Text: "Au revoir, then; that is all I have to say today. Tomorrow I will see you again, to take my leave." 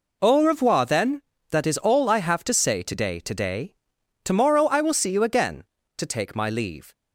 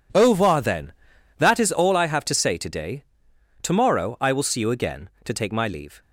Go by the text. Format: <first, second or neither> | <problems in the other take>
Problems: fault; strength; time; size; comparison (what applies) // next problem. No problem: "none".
second | says "today" twice; at 3.1 s